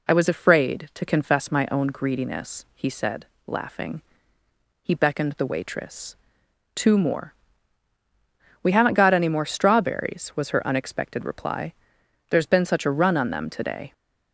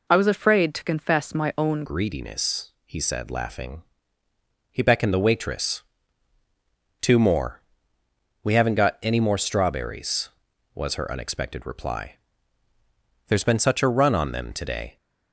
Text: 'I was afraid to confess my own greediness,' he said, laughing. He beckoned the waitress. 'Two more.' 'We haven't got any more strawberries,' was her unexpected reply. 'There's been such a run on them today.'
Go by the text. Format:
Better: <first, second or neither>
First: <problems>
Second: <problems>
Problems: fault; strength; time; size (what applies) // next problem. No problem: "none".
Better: first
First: none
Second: changes voice at "greediness"; from 1.8 s on; 13.1 s long